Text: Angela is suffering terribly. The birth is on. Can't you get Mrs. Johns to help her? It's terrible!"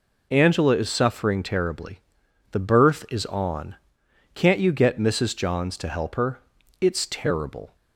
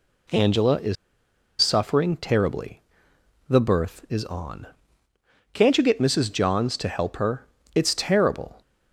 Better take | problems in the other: first | pauses between "is" and "suffering"; noticeable; at 0.9 s; 0.65 s long

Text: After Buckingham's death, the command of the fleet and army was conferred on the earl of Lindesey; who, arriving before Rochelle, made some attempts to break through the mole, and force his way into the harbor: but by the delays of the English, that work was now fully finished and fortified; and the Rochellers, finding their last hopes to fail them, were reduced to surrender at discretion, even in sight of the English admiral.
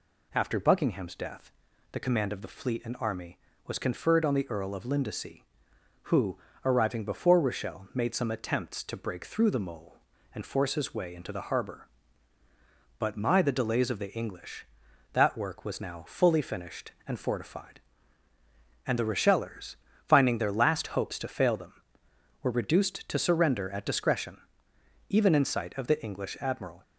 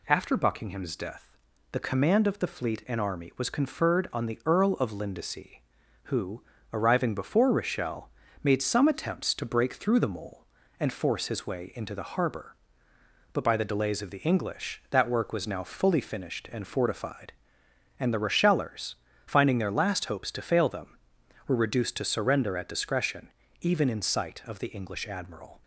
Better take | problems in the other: second | says "my" for "by"; at 13.1 s

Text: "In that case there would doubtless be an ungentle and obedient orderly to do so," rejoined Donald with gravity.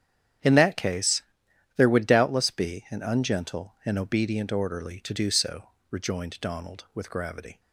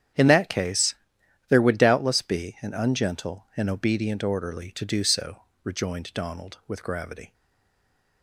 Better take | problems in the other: first | starts louder than the rest; strong; until 1.7 s; 9 dB; strong in the first // pauses between "case" and "there"; noticeable; at 0.9 s; 0.54 s long; noticeable in the first // stays silent after the last word; slight; from 7.3 s on; 0.9 s long

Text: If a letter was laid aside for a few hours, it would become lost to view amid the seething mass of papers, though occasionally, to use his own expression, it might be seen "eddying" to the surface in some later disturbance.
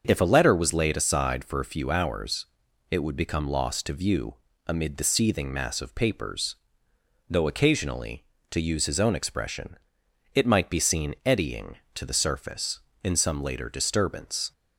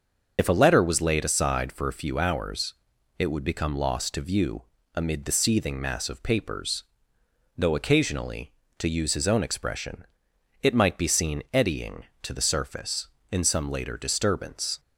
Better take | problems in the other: first | loses the start of "If"; at 0.3 s; 65 ms // starts louder than the rest; until 1.3 s; 6.5 dB; also in the first // pauses between "view" and "amid"; slight; at 4.6 s; 0.32 s long; slight in the first

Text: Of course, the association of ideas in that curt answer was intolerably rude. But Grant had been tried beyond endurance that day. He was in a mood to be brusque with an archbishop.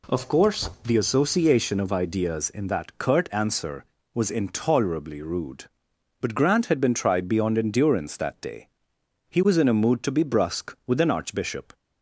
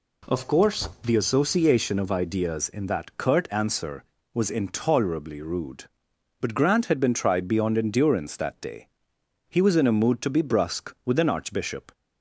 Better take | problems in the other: neither | none

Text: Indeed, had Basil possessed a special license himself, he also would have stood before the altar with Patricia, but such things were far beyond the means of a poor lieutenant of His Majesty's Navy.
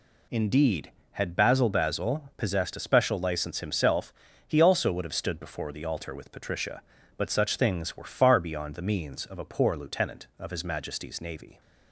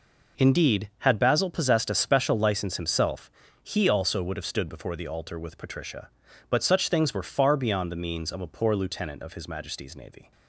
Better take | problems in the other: second | says "Basil" twice; at 1.6 s

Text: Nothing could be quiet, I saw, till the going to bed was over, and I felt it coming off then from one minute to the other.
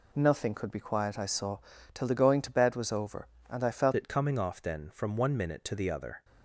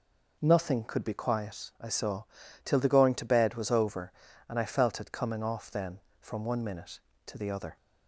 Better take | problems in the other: second | changes voice at "it"; from 3.9 s on; 2.3 s long

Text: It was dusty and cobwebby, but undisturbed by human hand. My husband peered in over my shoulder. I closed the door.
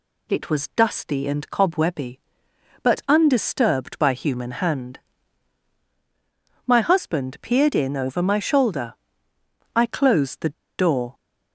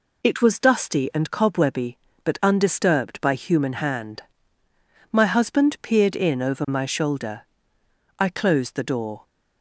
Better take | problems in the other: second | pauses between "the" and "door"; slight; at 10.5 s; 0.26 s long

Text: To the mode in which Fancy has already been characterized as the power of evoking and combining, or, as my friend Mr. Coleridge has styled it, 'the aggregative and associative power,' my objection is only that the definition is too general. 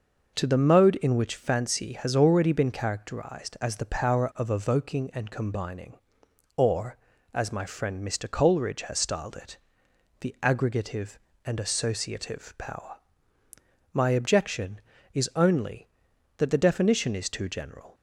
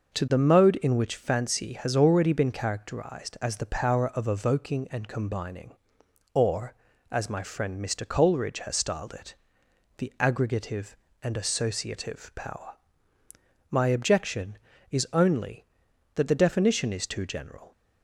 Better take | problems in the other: neither | none

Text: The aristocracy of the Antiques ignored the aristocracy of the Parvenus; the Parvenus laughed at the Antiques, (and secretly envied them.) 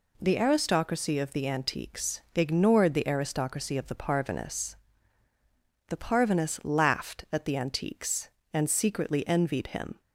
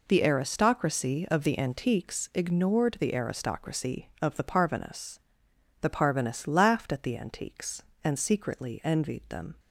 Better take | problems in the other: second | says "him" for "them"; at 9.6 s

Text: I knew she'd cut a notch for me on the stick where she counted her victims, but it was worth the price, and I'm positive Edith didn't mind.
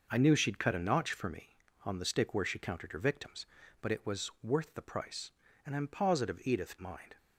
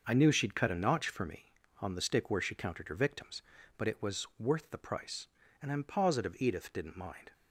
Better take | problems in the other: second | skips "didn't"; at 6.7 s

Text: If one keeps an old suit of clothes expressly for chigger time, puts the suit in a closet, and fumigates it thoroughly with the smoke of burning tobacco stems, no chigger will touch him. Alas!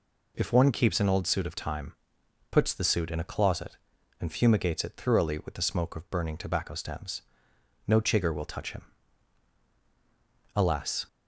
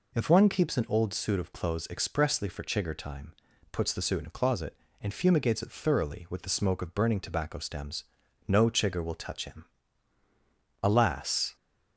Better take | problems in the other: second | skips "clothes expressly for chigger"; at 1.5 s

